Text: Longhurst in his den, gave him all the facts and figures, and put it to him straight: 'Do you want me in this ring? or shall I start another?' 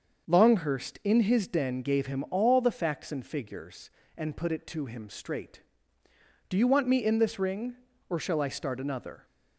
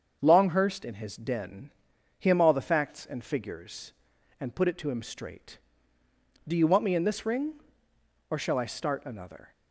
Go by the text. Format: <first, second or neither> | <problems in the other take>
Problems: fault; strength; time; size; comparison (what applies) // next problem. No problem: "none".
first | starts louder than the rest; until 1.2 s; 7 dB; also in the first // skips "gave"; at 1.9 s